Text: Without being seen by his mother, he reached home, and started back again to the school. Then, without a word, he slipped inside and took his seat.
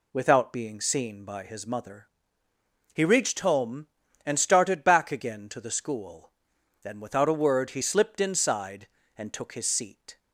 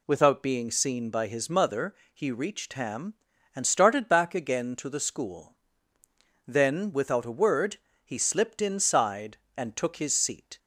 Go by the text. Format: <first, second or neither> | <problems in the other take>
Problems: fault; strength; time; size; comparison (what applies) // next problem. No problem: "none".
first | says "ham" for "home"; at 2.7 s